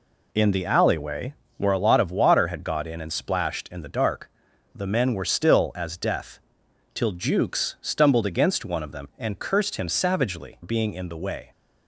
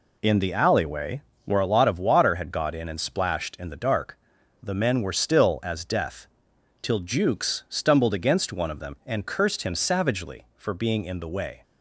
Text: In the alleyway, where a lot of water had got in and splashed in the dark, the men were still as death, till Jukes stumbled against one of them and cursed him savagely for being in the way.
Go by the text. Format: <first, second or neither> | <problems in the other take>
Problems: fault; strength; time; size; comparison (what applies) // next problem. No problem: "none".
second | skips "for"; at 10.6 s